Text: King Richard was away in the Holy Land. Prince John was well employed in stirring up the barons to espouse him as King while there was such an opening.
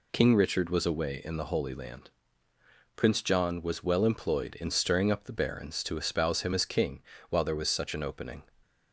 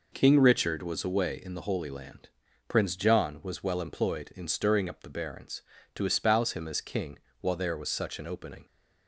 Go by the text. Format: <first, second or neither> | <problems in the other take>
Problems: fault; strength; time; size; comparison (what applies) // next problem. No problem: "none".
neither | pauses between "King" and "while"; slight; the same in both